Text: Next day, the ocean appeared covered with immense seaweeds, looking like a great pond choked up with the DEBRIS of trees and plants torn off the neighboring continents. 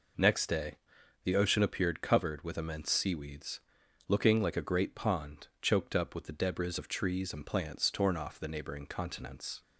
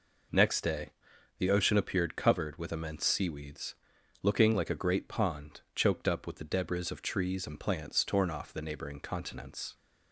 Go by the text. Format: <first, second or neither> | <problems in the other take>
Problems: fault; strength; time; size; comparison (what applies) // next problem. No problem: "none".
neither | pauses between "pond" and "choked"; slight; the same in both